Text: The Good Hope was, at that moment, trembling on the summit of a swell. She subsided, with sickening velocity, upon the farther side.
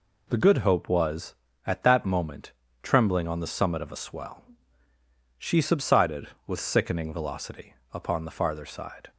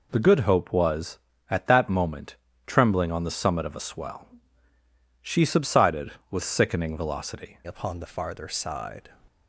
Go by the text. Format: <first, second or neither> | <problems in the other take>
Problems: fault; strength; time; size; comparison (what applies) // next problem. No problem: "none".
first | changes voice at "upon"; from 7.6 s on; 1.4 s long